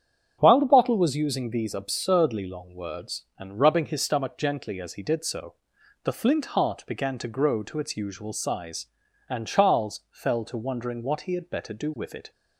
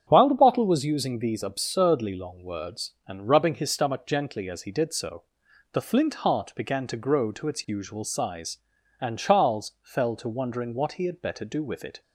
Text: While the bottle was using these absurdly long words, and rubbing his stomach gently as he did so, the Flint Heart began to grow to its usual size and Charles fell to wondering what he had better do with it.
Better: neither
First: starts louder than the rest; strong; until 1.4 s; 7.5 dB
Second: starts louder than the rest; strong; until 1.0 s; 7.5 dB

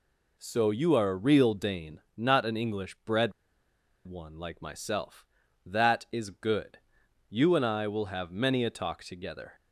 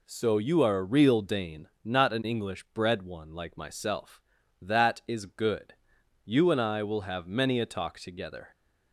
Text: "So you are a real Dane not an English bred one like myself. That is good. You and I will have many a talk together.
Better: second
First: pauses between "bred" and "one"; noticeable; at 3.3 s; 0.73 s long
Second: none

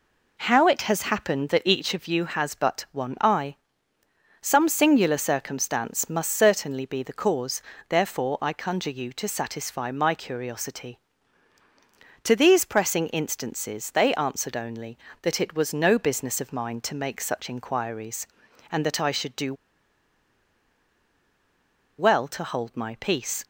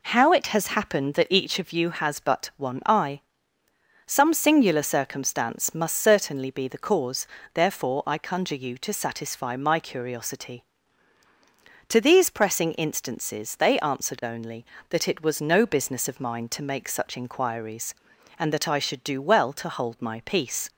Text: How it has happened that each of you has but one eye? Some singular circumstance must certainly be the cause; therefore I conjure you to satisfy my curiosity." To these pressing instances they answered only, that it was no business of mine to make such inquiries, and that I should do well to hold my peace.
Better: second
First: pauses between "do" and "well"; strong; at 19.5 s; 2.4 s long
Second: none

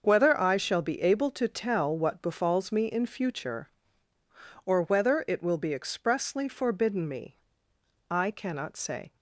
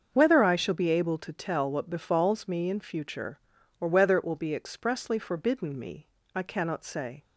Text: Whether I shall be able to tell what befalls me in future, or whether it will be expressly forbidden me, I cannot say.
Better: neither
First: starts louder than the rest; until 1.0 s; 6.5 dB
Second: starts louder than the rest; until 1.1 s; 6.5 dB

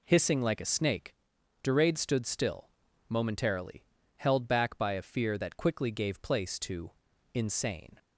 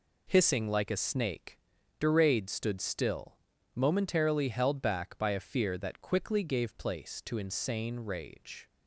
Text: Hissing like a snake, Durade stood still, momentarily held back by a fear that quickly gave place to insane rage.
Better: second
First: pauses between "momentarily" and "held"; slight; at 3.8 s; 0.30 s long // pauses between "to" and "insane"; at 6.9 s; 0.42 s long // stops before "rage"; at 7.9 s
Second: none

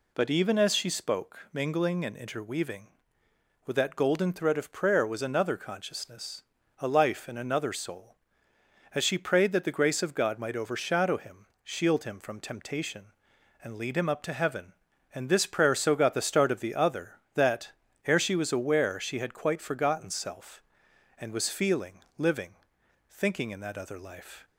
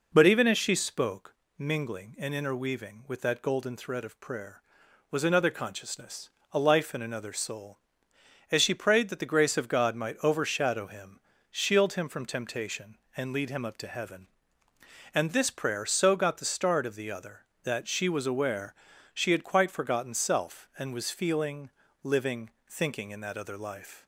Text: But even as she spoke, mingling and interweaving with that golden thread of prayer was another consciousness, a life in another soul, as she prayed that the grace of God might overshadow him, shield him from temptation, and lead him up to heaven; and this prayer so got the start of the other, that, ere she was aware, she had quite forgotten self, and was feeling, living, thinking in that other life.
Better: first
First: none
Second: skips "ere"; at 17.8 s

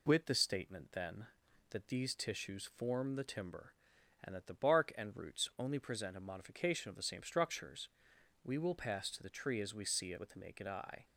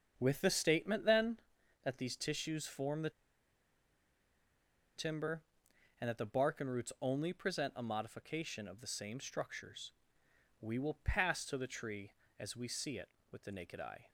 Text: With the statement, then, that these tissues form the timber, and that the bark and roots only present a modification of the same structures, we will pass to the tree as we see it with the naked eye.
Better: first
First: none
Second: starts louder than the rest; until 1.1 s; 7 dB // pauses between "the" and "timber"; strong; at 3.0 s; 1.8 s long

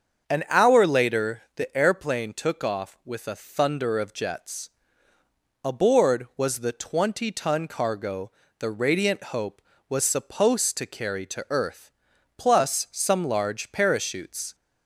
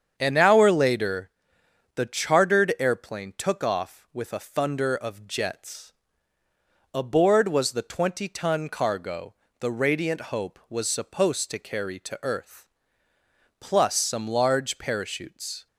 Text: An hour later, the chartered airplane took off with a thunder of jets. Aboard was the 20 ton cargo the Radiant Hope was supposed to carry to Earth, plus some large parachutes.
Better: second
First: starts louder than the rest; until 1.3 s; 7 dB // skips "chartered"; at 1.7 s // pauses between "cargo" and "the"; slight; at 8.3 s; 0.26 s long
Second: starts louder than the rest; strong; until 1.1 s; 7.5 dB // pauses between "cargo" and "the"; slight; at 9.3 s; 0.24 s long

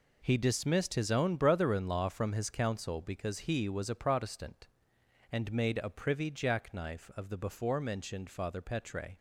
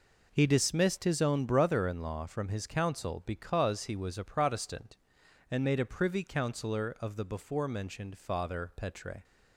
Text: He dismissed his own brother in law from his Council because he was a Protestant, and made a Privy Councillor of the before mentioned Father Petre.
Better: second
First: says "Jackknife" for "Councillor"; at 6.3 s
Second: none

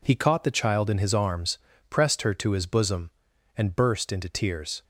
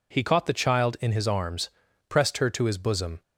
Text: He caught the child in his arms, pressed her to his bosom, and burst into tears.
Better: first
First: none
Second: stops before "and burst into tears"; at 3.2 s

